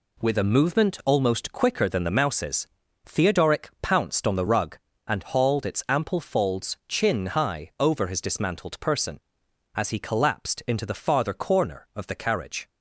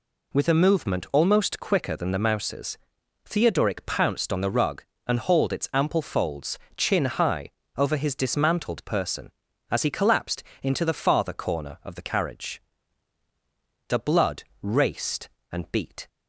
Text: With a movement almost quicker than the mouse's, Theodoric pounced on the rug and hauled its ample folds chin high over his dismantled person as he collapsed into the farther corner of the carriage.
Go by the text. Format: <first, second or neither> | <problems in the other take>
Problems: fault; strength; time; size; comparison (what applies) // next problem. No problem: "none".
first | pauses between "folds" and "chin"; slight; at 6.5 s; 0.18 s long // pauses between "high" and "over"; slight; at 7.4 s; 0.26 s long // pauses between "collapsed" and "into"; slight; at 10.4 s; 0.18 s long // goes on to say "The blood raced and beat"; strong; from 13.8 s on; 2.2 s long